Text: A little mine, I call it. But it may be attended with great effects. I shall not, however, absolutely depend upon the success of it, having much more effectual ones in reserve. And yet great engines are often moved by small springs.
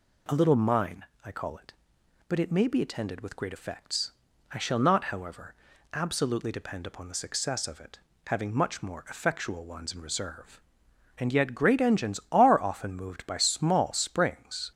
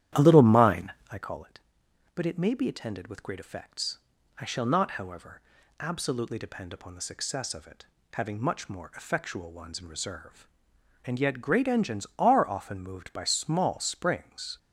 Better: first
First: none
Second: starts louder than the rest; strong; until 1.3 s; 11.5 dB

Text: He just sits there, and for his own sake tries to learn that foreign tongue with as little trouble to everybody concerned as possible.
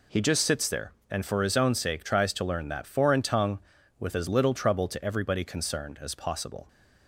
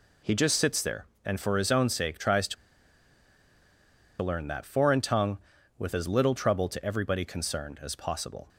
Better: first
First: none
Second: pauses between "to" and "learn"; strong; at 2.5 s; 1.6 s long

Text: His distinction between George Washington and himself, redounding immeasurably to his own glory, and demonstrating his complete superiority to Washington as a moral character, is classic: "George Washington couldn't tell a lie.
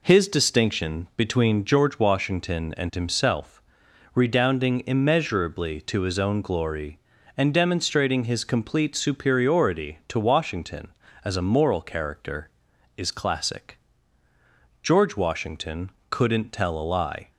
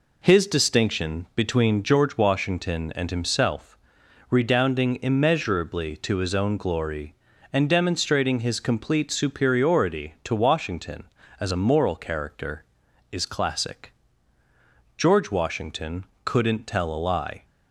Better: neither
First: pauses between "Washington" and "couldn't"; slight; at 15.9 s; 0.18 s long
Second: pauses between "Washington" and "couldn't"; slight; at 16.0 s; 0.18 s long

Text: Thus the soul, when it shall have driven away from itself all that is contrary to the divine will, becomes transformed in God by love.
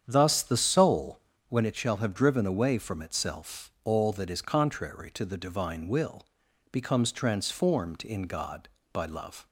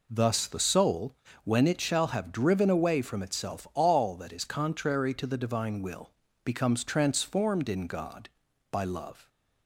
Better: second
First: starts louder than the rest; strong; until 1.5 s; 8.5 dB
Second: none

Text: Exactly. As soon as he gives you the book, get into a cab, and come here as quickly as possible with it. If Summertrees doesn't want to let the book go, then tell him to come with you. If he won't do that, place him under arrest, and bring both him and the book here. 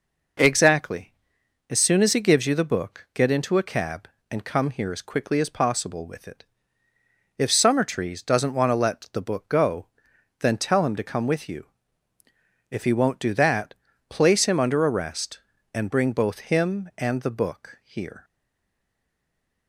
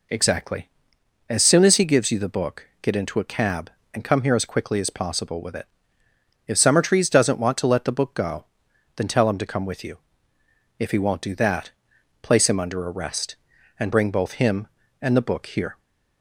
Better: second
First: stays silent after the last word; noticeable; from 18.2 s on; 1.4 s long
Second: none

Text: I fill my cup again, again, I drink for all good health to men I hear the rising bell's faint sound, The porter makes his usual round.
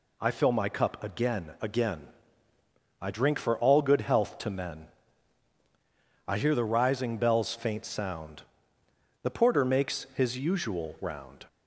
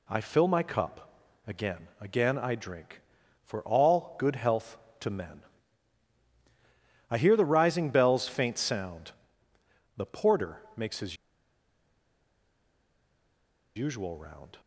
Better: first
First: pauses between "men" and "I"; strong; at 4.8 s; 1.4 s long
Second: pauses between "cup" and "again"; slight; at 1.1 s; 0.34 s long // pauses between "men" and "I"; strong; at 5.4 s; 1.6 s long // pauses between "porter" and "makes"; slight; at 10.5 s; 0.16 s long // pauses between "his" and "usual"; strong; at 11.1 s; 2.6 s long

